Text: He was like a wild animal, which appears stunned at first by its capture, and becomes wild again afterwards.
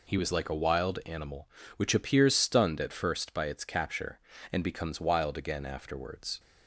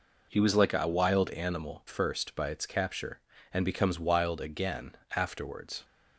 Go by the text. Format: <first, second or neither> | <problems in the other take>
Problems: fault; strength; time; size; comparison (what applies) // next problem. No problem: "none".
first | skips "which appears stunned at"; at 1.8 s // pauses between "again" and "afterwards"; slight; at 4.9 s; 0.20 s long